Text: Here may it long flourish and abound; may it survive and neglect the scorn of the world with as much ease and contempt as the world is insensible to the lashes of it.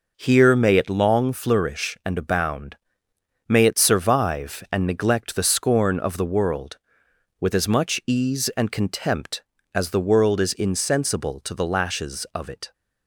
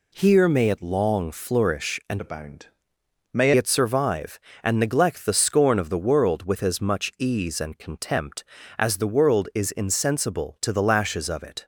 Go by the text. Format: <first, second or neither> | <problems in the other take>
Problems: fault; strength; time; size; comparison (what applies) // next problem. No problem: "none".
first | changes voice from "abound" to "may"; from 2.2 to 3.5 s; 1.3 s long